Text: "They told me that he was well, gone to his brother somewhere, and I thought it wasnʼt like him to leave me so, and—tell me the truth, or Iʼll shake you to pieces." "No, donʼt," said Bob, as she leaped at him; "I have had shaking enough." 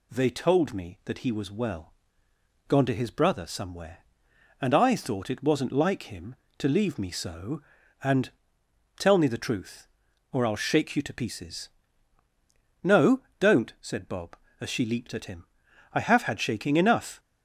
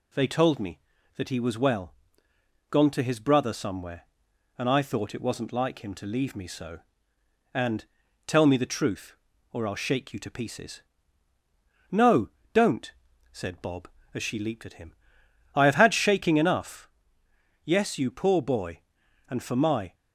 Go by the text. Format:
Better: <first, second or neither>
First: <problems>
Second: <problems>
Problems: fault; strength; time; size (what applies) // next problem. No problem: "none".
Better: first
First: none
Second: goes on to say "Yes you poor boy and for my"; strong; from 17.6 s on; 2.3 s long